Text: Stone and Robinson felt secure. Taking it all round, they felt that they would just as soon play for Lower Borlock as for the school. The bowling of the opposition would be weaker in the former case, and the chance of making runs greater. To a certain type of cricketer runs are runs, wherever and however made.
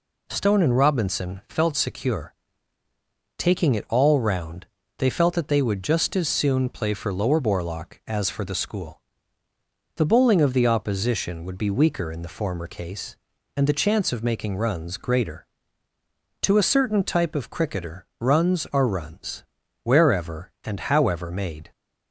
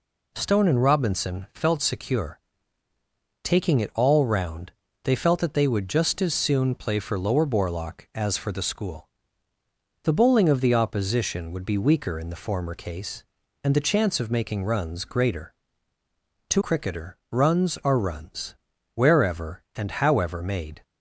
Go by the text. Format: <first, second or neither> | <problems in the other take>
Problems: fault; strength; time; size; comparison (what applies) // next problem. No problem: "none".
first | skips "a certain type of"; at 16.6 s